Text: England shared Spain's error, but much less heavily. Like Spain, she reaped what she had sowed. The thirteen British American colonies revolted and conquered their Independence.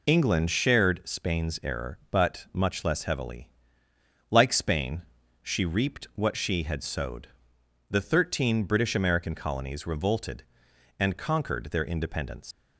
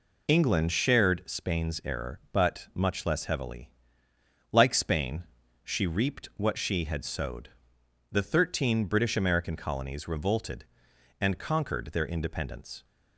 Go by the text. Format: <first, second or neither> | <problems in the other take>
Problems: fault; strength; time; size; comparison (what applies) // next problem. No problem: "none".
second | leaves "Independence" unfinished; at 12.5 s; 125 ms